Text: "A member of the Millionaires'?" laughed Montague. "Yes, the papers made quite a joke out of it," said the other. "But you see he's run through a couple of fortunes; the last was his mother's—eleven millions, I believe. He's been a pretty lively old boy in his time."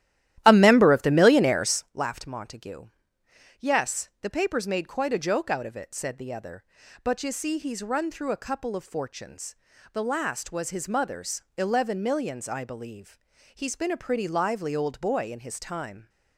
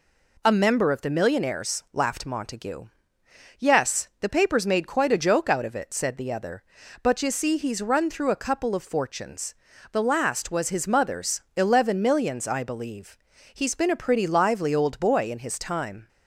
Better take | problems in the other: second | starts louder than the rest; strong; until 1.9 s; 13 dB

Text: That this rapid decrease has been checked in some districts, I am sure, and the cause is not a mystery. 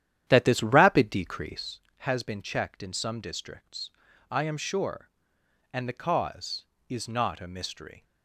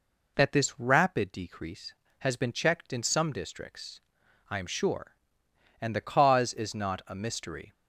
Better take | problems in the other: second | starts louder than the rest; strong; until 1.8 s; 10.5 dB

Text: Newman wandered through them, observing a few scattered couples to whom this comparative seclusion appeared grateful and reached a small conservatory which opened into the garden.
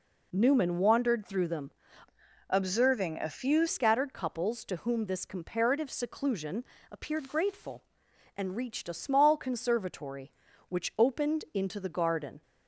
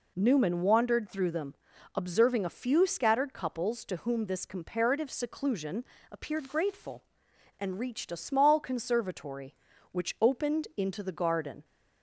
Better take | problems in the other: second | changes voice from "observing" to "few"; from 2.4 to 3.6 s; 1.2 s long // pauses between "seclusion" and "appeared"; slight; at 6.6 s; 0.26 s long; slight in the second

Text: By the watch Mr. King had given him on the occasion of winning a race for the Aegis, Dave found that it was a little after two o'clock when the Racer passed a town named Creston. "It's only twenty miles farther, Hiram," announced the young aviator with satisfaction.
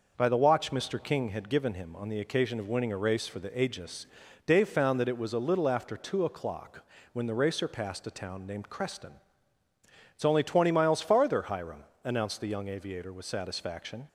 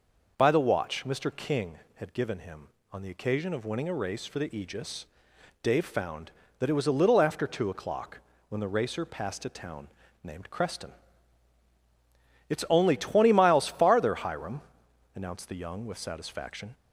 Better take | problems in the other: first | pauses between "o'clock" and "when"; slight; at 8.1 s; 0.30 s long; slight in the first // pauses between "town" and "named"; slight; at 9.8 s; 0.36 s long // skips "aviator"; at 15.8 s

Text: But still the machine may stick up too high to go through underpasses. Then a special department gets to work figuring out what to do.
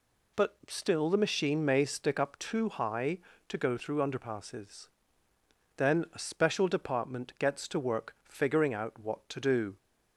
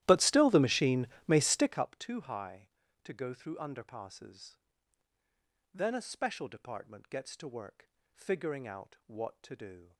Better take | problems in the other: first | starts louder than the rest; strong; until 1.8 s; 14 dB // pauses between "machine" and "may"; slight; at 1.0 s; 0.20 s long // pauses between "work" and "figuring"; slight; at 7.8 s; 0.24 s long

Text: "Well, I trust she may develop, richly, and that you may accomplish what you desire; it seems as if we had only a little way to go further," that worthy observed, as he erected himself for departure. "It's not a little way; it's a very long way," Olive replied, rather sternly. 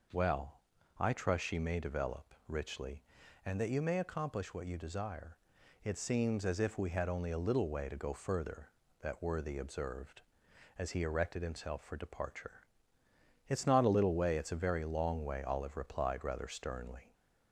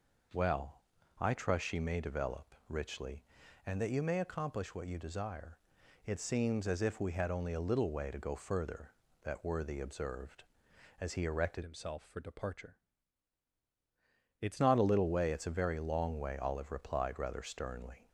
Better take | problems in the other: first | changes voice from "himself" to "It's"; from 11.6 to 14.6 s; 3.0 s long

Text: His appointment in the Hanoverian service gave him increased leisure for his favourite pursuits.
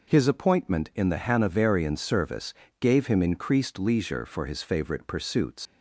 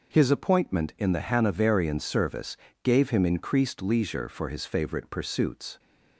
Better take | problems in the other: second | pauses between "service" and "gave"; slight; at 2.5 s; 0.26 s long; slight in the second // leaves "pursuits" unfinished; at 5.6 s; 100 ms

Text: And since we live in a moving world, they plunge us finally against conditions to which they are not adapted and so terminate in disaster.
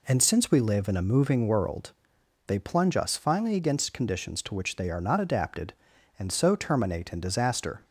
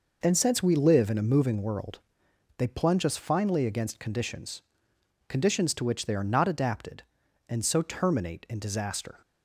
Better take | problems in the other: first | says "conditions" twice; at 5.2 s

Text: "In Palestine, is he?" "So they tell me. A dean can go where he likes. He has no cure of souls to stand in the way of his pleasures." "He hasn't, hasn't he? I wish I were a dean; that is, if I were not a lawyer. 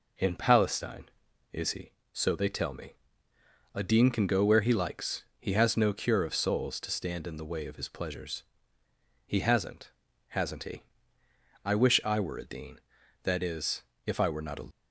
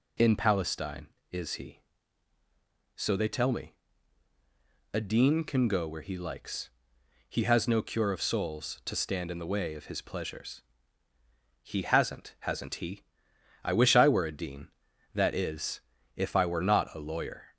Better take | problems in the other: second | stops before "lawyer"; at 14.7 s

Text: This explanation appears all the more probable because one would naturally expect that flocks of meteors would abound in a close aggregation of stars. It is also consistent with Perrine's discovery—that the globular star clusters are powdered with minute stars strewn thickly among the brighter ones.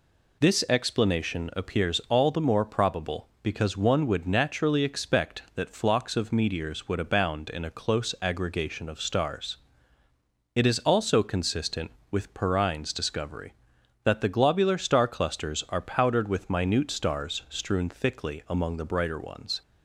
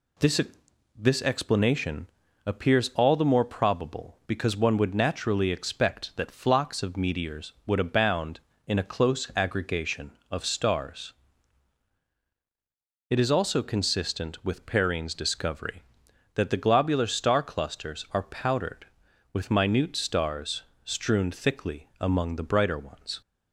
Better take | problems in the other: first | says "This" twice; at 0.9 s // pauses between "explanation" and "appears"; at 2.0 s; 0.40 s long // pauses between "stars" and "strewn"; slight; at 20.6 s; 0.22 s long

